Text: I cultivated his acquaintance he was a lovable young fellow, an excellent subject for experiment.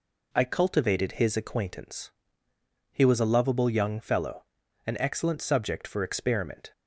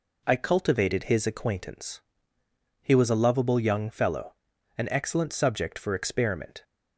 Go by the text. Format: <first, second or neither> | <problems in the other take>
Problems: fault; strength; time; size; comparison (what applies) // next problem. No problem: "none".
neither | pauses between "acquaintance" and "he"; noticeable; the same in both